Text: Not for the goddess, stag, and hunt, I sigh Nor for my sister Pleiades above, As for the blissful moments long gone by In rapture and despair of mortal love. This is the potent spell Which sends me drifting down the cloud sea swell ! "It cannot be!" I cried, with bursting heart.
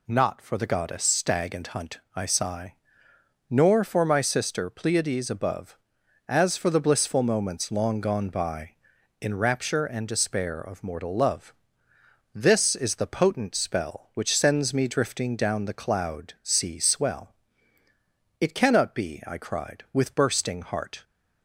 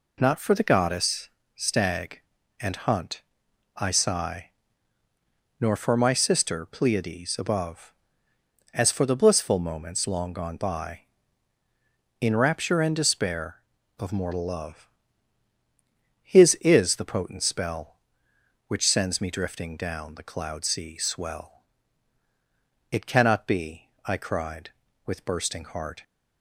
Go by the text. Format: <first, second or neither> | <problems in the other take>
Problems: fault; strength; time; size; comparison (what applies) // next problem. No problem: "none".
first | pauses between "sigh" and "Nor"; at 4.5 s; 1.1 s long; noticeable in the first // says "His" for "This"; at 16.2 s